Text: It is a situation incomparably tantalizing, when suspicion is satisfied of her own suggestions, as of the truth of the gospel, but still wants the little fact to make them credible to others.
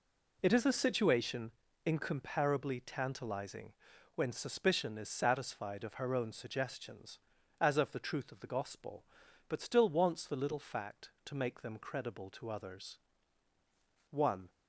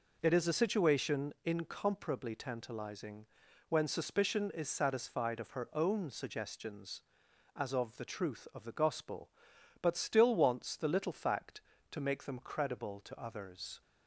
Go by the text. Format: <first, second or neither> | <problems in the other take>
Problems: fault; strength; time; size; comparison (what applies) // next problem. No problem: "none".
second | pauses between "situation" and "incomparably"; slight; at 1.5 s; 0.34 s long // goes on to say "One"; slight; from 14.1 s on; 0.38 s long